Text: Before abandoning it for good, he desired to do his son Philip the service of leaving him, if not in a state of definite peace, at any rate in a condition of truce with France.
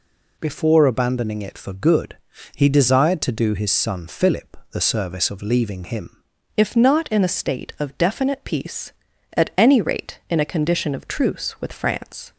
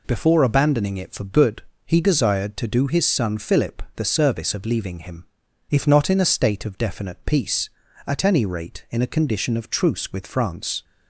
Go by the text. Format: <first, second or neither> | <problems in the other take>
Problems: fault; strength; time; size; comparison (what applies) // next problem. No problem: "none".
second | changes voice at "if"; from 6.5 s on; 5.8 s long